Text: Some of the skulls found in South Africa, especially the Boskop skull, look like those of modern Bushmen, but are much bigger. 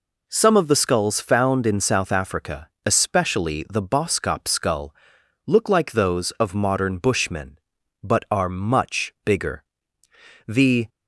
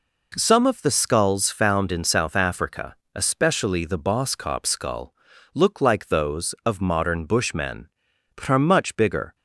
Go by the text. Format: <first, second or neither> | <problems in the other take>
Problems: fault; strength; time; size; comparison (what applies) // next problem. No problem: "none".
second | goes on to say "The"; slight; from 10.4 s on; 0.42 s long